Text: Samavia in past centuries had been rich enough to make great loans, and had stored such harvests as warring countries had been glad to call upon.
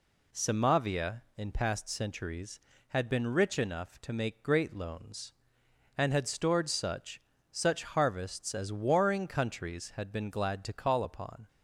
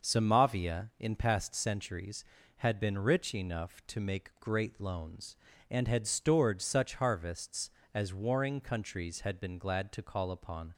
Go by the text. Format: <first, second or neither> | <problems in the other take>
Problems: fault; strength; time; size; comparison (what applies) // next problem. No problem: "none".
second | says "such" twice; at 7.5 s